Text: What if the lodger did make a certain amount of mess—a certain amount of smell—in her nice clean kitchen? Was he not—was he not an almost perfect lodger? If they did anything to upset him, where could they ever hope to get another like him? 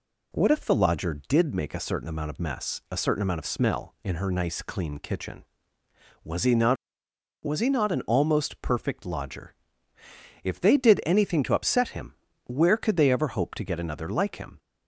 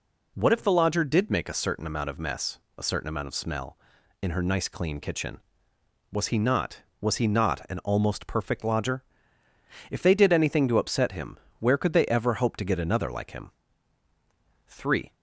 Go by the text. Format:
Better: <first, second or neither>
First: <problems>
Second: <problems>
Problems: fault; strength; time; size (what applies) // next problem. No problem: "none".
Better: first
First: none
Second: goes on to say "Three"; slight; from 14.6 s on; 0.48 s long